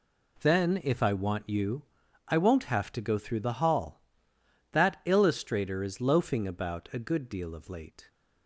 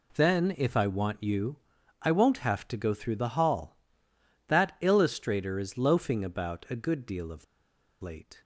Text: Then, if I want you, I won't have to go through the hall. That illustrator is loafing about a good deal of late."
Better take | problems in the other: first | pauses between "of" and "late"; noticeable; at 7.4 s; 0.58 s long

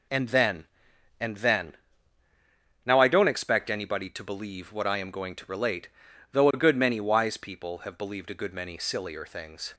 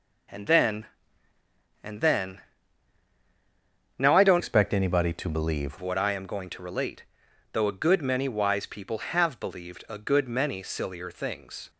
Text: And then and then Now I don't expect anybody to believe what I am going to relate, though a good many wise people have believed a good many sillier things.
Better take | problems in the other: first | pauses between "then" and "Now"; strong; at 2.3 s; 1.5 s long; also in the first // changes voice from "expect" to "believe"; from 4.3 to 5.7 s; 1.4 s long

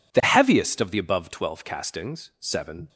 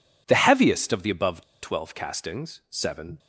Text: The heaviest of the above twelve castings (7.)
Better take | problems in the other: first | pauses between "above" and "twelve"; slight; at 1.4 s; 0.20 s long

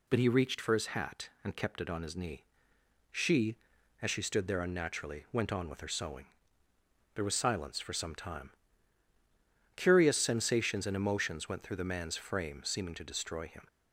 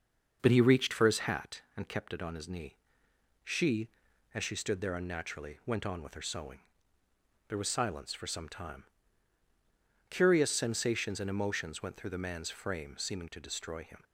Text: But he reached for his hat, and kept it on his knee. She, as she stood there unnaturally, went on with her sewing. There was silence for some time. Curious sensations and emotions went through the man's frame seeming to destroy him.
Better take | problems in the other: first | starts louder than the rest; until 1.5 s; 6 dB

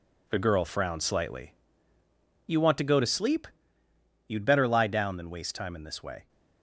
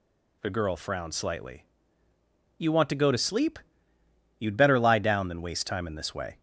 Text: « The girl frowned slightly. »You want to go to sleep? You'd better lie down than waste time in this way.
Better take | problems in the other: second | gets quieter; strong; throughout; 8 dB

